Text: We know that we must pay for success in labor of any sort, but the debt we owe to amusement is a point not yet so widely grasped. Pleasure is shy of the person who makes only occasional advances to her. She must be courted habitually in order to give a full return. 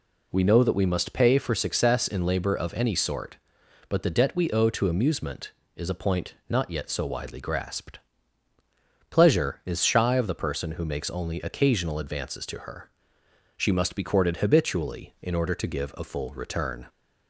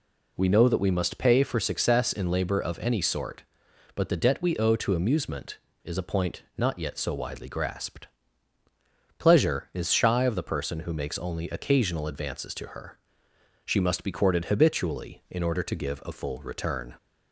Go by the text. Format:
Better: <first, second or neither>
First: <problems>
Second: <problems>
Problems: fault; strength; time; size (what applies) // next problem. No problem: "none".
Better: neither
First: none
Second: none